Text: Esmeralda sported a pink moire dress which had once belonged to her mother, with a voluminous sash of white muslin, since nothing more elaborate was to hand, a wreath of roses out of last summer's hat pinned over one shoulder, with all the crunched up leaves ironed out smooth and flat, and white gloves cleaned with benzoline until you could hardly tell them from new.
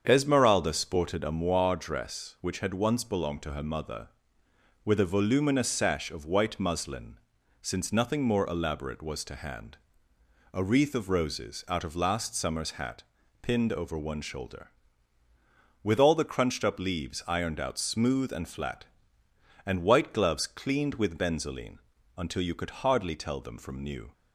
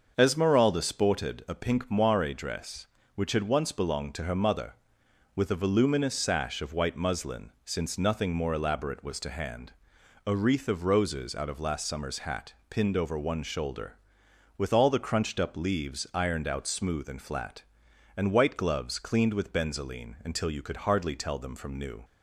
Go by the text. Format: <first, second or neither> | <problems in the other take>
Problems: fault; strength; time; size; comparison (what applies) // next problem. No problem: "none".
second | starts louder than the rest; strong; until 1.0 s; 7.5 dB; also in the second // skips "pink"; at 1.3 s // pauses between "hat" and "pinned"; at 13.0 s; 0.40 s long; slight in the second // pauses between "benzoline" and "until"; slight; at 21.7 s; 0.36 s long